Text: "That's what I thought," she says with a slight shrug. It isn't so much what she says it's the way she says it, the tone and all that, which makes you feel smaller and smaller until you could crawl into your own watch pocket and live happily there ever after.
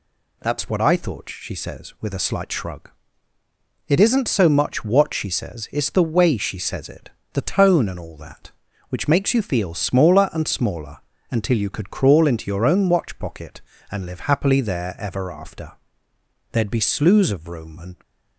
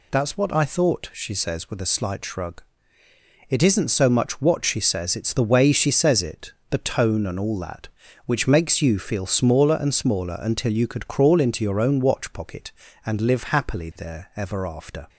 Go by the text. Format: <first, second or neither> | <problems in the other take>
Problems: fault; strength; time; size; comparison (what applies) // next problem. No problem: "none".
second | pauses between "smaller" and "until"; slight; at 10.9 s; 0.32 s long // goes on to say "There'd be slews of room and"; from 16.5 s on; 1.4 s long